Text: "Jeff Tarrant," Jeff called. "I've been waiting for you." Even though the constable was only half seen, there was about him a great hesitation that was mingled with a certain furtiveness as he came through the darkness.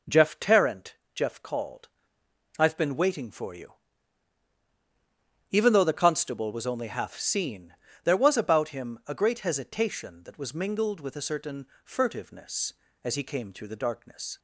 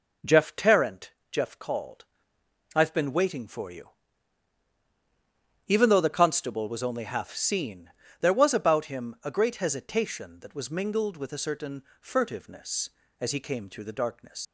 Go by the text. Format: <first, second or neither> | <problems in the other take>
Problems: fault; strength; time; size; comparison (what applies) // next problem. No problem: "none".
first | pauses between "certain" and "furtiveness"; slight; at 11.8 s; 0.18 s long; slight in the first // leaves "darkness" unfinished; at 14.4 s; 100 ms